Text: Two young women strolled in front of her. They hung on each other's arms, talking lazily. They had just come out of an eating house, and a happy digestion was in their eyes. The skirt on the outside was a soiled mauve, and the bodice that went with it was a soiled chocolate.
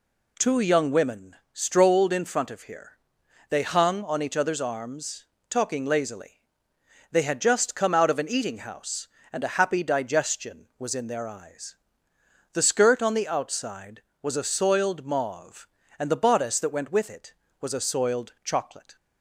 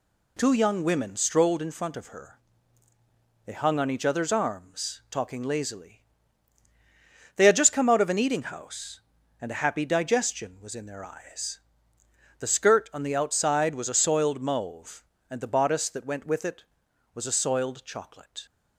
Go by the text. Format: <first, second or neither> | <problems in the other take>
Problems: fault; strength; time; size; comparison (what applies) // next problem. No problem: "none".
second | pauses between "women" and "strolled"; slight; at 1.3 s; 0.18 s long // says "here" for "her"; at 2.6 s